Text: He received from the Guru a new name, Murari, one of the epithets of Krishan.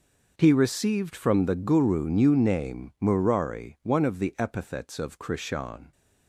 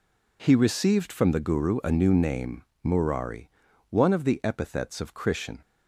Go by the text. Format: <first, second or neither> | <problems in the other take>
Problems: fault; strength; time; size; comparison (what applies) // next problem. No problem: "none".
second | skips "a"; at 2.0 s